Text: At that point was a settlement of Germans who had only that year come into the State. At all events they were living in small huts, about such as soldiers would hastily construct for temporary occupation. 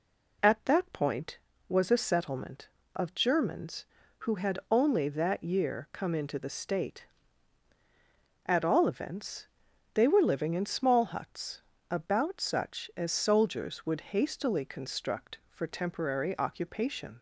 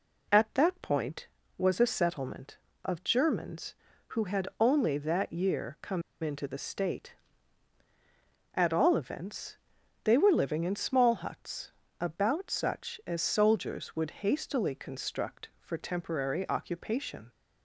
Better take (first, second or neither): first